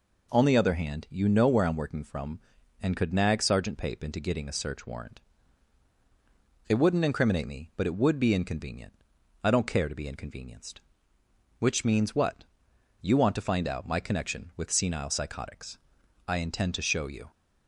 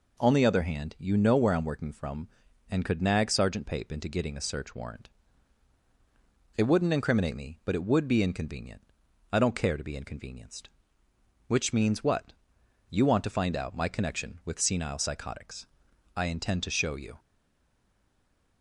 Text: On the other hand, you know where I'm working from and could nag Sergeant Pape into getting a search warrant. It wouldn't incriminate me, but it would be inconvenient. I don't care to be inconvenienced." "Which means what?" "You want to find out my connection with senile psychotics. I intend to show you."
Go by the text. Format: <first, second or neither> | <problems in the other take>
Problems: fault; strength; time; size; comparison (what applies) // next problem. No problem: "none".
first | stays silent after the last word; noticeable; from 17.1 s on; 1.5 s long